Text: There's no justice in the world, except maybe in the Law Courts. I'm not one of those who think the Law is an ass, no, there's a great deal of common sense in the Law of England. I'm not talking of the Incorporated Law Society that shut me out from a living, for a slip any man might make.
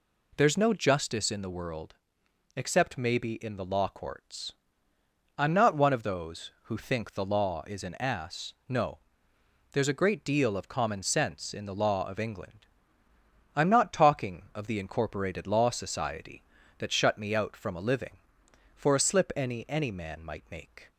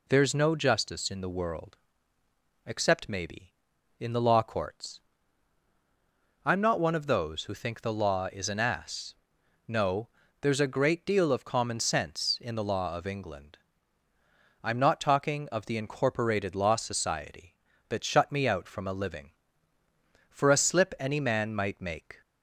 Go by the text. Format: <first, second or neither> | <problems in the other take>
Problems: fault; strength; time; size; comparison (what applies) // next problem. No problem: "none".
second | says "any" twice; at 19.6 s